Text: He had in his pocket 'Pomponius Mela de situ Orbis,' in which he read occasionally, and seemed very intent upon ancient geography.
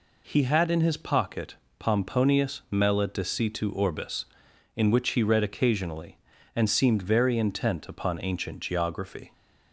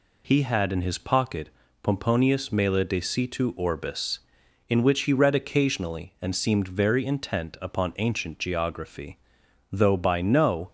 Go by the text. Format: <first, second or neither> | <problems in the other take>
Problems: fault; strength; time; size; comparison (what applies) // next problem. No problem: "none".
first | pauses between "pocket" and "Pomponius"; slight; at 1.4 s; 0.34 s long; slight in the first // goes on to say "Though by no"; noticeable; from 9.6 s on; 1.0 s long